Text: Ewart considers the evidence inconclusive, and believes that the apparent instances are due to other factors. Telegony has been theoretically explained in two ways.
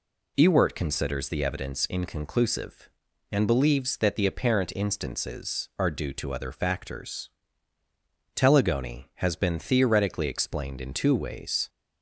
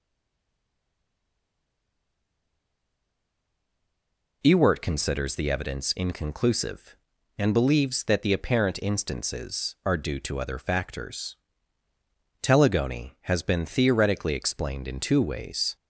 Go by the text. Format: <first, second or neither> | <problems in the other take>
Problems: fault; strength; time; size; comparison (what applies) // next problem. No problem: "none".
first | stays silent before the first word; strong; until 4.4 s; 4.4 s long